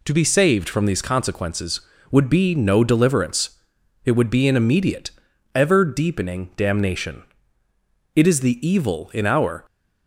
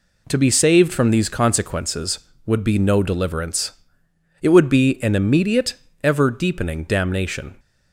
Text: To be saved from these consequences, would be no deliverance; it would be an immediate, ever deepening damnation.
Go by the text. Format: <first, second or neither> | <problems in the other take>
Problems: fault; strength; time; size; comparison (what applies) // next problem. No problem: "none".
second | goes on to say "It is the evil in our"; from 8.1 s on; 1.4 s long